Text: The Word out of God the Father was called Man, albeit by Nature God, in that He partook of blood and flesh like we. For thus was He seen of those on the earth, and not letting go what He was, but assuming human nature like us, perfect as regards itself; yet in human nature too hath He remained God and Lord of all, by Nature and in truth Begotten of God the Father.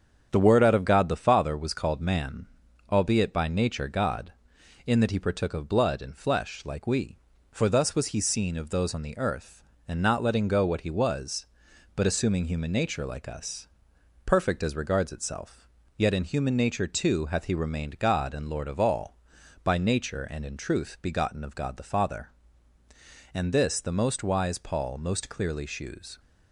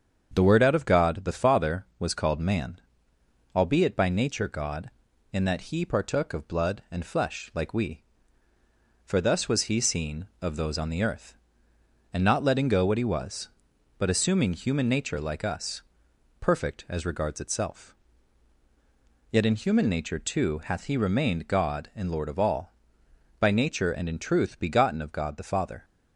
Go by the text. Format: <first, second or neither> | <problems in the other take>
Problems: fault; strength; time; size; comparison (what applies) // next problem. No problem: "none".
second | starts louder than the rest; strong; until 1.3 s; 8 dB; strong in the second // goes on to say "And this the most wise Paul most clearly shews"; strong; from 23.3 s on; 2.8 s long